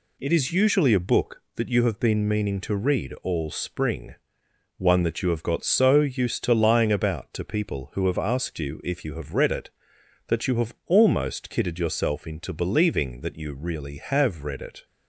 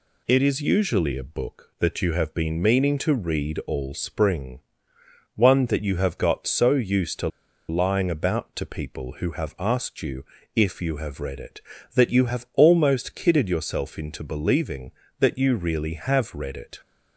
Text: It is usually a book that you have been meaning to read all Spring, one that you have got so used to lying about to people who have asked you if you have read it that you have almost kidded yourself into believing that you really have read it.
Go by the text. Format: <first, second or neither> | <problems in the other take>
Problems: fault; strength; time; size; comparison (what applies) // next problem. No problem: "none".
first | pauses between "to" and "lying"; at 7.2 s; 0.41 s long // pauses between "you" and "if"; slight; at 10.2 s; 0.30 s long